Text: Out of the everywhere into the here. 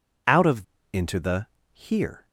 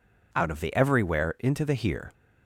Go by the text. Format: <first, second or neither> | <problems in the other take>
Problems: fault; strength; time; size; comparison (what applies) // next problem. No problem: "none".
second | skips "the everywhere"; at 0.7 s // pauses between "the" and "here"; slight; at 1.4 s; 0.26 s long